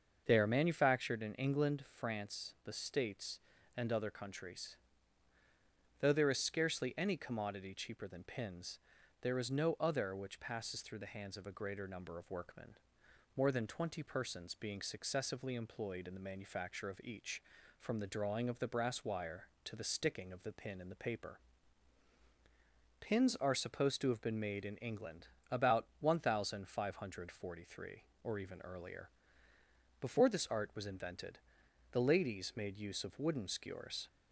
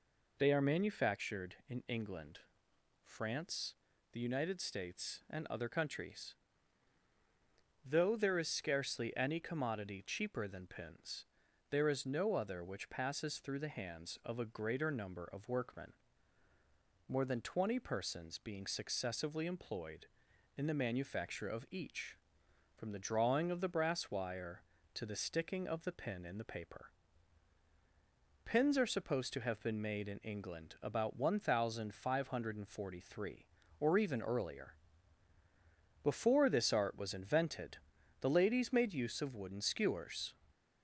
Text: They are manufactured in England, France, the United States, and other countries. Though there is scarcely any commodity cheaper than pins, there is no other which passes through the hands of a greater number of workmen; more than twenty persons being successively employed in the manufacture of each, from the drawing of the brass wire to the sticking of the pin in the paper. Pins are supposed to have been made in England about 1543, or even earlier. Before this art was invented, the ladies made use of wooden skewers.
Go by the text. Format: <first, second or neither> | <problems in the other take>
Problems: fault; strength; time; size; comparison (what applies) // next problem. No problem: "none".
second | starts louder than the rest; until 1.2 s; 6.5 dB // skips "United"; at 2.7 s // pauses between "England" and "about"; slight; at 25.2 s; 0.22 s long